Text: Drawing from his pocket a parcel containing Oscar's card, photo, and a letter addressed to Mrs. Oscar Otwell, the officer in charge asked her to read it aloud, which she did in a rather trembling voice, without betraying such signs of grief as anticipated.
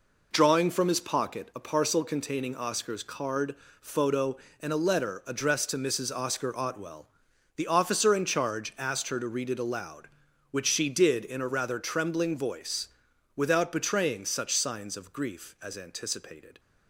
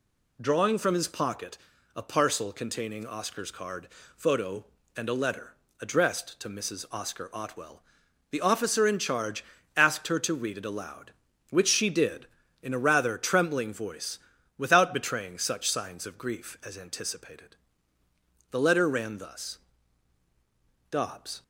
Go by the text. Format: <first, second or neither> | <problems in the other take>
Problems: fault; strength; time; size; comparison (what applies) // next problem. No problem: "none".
first | pauses between "pocket" and "a"; at 1.5 s; 0.38 s long // pauses between "letter" and "addressed"; slight; at 5.5 s; 0.26 s long // pauses between "charge" and "asked"; slight; at 9.4 s; 0.32 s long // goes on to say "The letter ran thus Dobbs"; strong; from 18.5 s on; 2.9 s long